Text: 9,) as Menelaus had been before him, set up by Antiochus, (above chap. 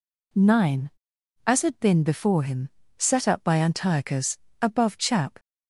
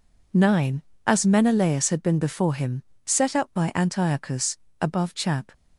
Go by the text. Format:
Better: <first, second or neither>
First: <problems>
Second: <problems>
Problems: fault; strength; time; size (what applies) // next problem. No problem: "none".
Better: second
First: skips "Menelaus"; at 1.6 s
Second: none